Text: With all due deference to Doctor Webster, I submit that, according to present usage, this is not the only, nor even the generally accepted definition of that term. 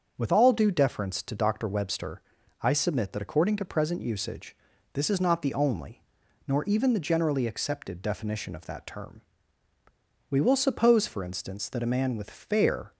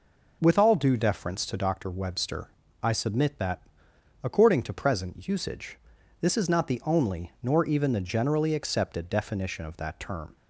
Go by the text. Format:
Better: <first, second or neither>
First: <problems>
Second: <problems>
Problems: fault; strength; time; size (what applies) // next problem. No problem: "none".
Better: second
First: starts louder than the rest; until 1.1 s; 6.5 dB // goes on to say "We will suppose for instance that a man with fair"; strong; from 10.3 s on; 2.6 s long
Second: none